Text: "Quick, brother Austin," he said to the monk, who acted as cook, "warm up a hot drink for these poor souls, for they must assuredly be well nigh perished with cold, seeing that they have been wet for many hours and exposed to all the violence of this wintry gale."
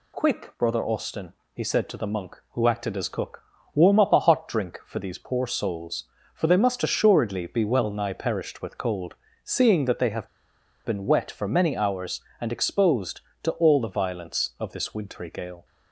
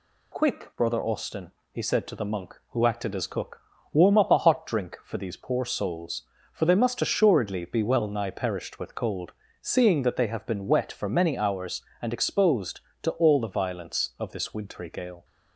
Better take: second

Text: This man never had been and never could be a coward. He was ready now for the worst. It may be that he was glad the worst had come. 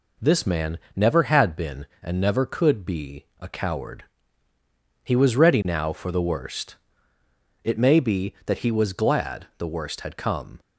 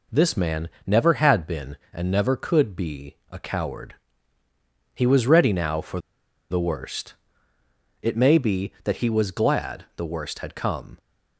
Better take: first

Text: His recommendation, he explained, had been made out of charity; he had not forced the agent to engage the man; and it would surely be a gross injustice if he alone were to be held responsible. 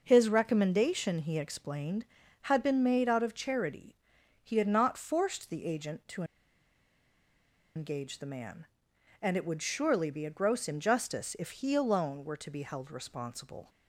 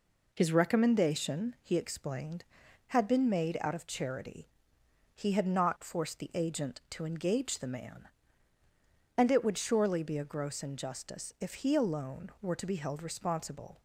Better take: second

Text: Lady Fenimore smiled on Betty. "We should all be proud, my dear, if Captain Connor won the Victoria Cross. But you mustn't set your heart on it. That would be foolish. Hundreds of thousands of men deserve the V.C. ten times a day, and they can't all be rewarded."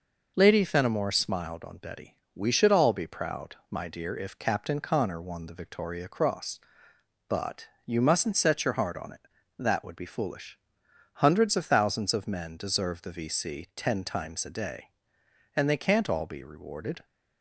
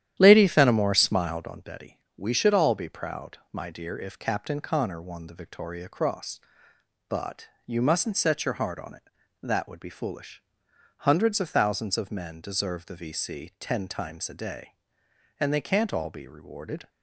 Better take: first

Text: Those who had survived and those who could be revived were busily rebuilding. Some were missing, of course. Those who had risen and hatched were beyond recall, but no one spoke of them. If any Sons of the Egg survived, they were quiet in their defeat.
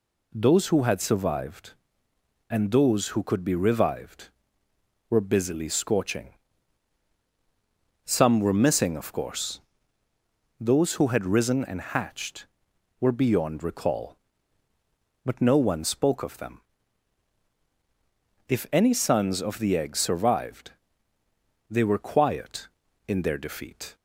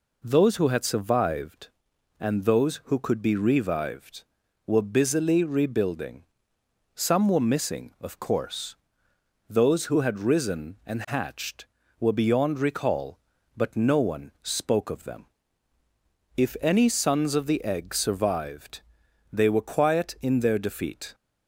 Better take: second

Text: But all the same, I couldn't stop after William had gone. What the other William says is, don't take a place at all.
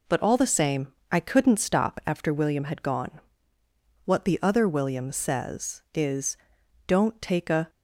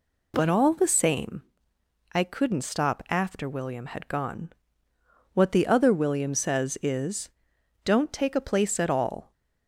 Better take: second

